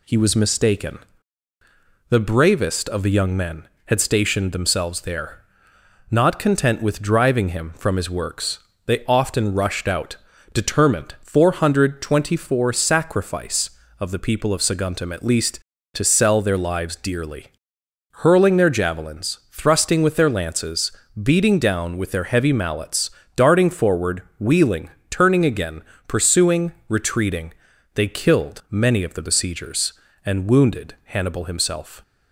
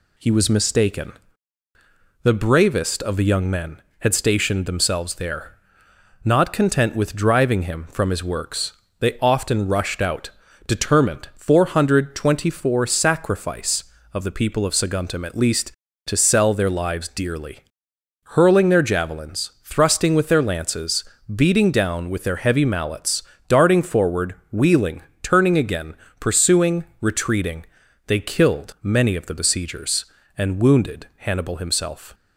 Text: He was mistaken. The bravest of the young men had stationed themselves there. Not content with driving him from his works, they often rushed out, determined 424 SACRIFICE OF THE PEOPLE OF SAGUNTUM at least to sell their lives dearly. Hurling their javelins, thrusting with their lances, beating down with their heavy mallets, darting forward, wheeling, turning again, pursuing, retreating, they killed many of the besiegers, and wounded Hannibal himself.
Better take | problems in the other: neither | none

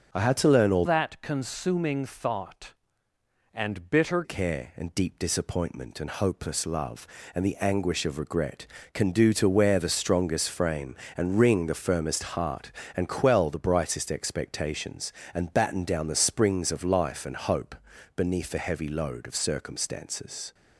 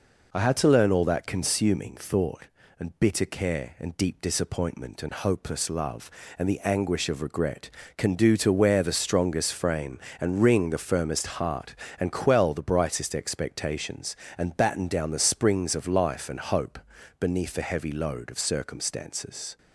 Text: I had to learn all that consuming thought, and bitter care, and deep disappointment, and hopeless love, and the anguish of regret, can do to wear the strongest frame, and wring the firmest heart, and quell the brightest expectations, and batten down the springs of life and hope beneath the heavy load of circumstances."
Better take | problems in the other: second | starts louder than the rest; noticeable; until 1.2 s; 6 dB // changes voice from "that" to "bitter"; from 0.8 to 4.2 s; 3.4 s long // pauses between "hope" and "beneath"; at 17.7 s; 0.40 s long; also in the second

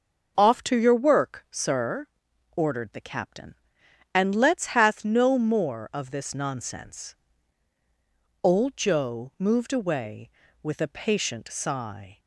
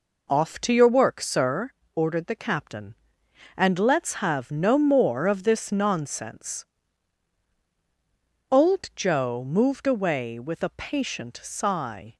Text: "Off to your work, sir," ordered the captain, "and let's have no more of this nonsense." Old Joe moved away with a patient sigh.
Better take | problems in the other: second | starts louder than the rest; until 1.3 s; 6 dB // says "hath" for "have"; at 4.6 s

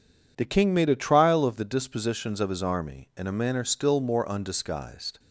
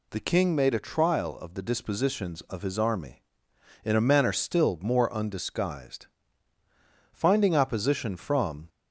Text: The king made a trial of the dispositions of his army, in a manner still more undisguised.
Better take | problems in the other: first | goes on to say "Finding opposition from"; from 7.1 s on; 1.5 s long

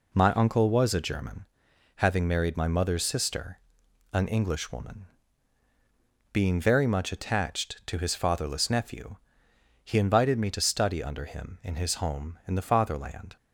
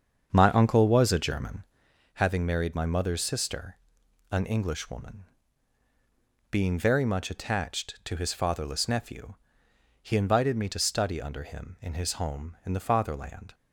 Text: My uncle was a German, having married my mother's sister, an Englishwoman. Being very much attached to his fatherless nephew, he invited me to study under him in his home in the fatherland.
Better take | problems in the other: first | starts louder than the rest; strong; until 1.9 s; 7 dB

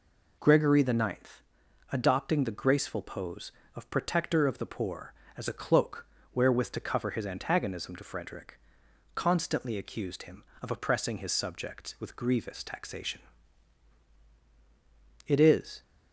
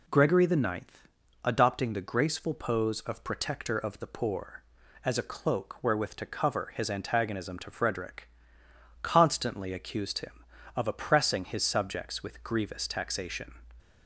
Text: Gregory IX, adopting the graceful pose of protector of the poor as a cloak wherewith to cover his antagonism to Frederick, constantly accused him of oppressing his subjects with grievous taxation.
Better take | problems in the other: second | pauses between "cloak" and "wherewith"; slight; at 6.0 s; 0.28 s long // goes on to say "It is"; from 15.2 s on; 0.56 s long

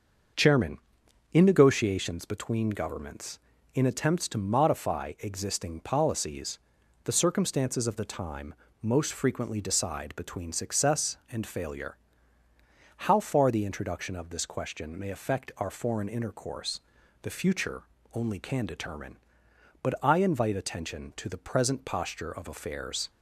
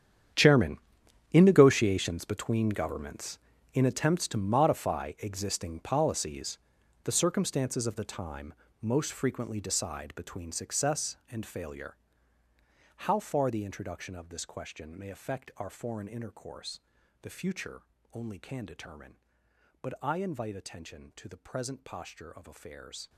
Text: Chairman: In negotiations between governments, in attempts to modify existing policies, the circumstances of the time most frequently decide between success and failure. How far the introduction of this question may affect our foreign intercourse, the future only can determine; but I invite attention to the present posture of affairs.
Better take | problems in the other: first | gets quieter; strong; throughout; 16.5 dB // starts louder than the rest; strong; until 1.8 s; 9 dB; also in the first // pauses between "time" and "most"; slight; at 8.5 s; 0.26 s long; slight in the first // pauses between "future" and "only"; slight; at 17.8 s; 0.28 s long; slight in the first

